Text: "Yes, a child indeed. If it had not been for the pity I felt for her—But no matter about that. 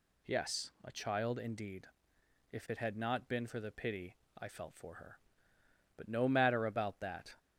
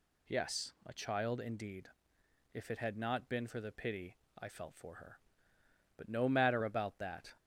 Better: neither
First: pauses between "pity" and "I"; slight; at 4.1 s; 0.20 s long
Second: pauses between "pity" and "I"; slight; at 4.1 s; 0.20 s long

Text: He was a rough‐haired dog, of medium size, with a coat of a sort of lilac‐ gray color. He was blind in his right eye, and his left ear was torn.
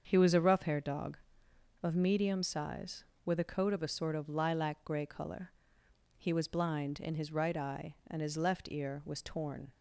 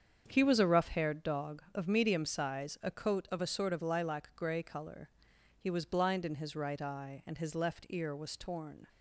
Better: first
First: starts louder than the rest; until 1.1 s; 7 dB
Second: starts louder than the rest; strong; until 1.2 s; 7.5 dB // skips "with"; at 2.7 s

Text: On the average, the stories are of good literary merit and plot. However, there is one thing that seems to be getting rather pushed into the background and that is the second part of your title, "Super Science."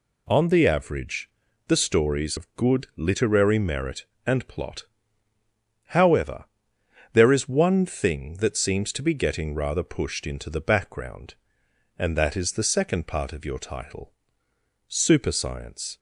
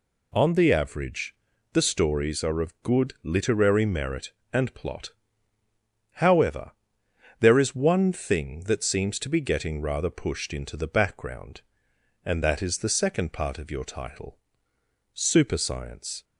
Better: second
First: skips "are"; at 2.3 s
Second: none

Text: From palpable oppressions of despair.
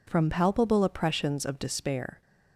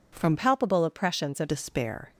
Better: first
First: none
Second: changes voice from "palpable" to "of"; from 0.3 to 1.4 s; 1.1 s long

